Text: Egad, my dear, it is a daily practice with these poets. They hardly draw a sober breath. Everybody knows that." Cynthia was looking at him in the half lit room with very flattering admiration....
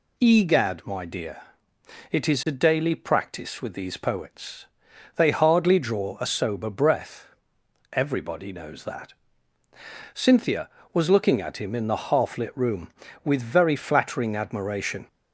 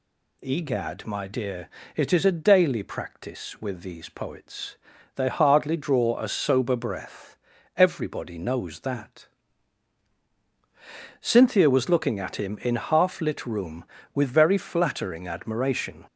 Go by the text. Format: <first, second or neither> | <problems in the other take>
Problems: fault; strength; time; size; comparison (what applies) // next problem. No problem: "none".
first | skips "the"; at 12.7 s